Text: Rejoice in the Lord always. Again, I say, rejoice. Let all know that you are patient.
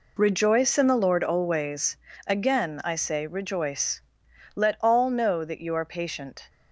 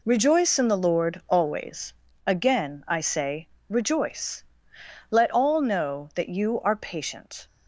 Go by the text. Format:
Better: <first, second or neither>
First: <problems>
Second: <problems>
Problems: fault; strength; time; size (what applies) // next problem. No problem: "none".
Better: neither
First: none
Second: none